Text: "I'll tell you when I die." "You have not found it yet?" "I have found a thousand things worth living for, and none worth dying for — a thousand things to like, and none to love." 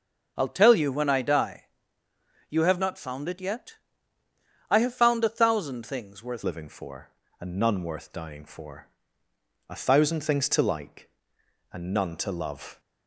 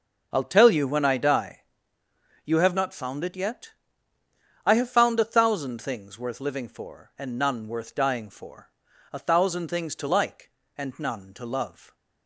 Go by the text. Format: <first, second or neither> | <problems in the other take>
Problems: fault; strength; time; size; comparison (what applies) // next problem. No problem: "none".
second | starts louder than the rest; until 1.3 s; 7 dB; also in the second // changes voice at "living"; from 6.4 s on; 6.3 s long